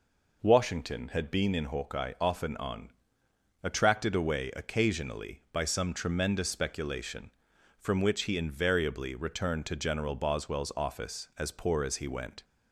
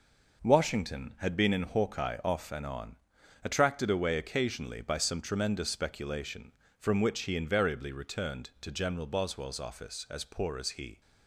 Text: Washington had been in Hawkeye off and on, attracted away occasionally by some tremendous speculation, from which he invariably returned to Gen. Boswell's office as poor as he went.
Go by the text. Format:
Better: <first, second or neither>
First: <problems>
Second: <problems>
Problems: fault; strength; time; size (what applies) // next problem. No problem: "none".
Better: first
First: none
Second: stops before "went"; at 11.0 s